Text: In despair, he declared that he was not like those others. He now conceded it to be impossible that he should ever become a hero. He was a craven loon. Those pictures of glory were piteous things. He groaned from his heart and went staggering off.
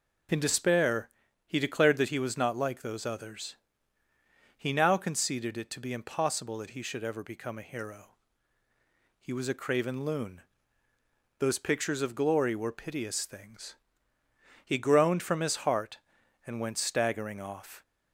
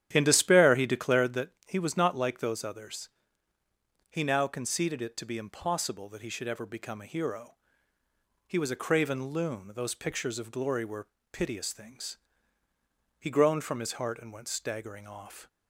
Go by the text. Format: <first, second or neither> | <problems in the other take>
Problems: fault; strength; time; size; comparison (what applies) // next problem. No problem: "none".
first | starts louder than the rest; strong; until 1.4 s; 10.5 dB // pauses between "that" and "he"; slight; at 1.5 s; 0.16 s long // pauses between "were" and "piteous"; slight; at 11.0 s; 0.24 s long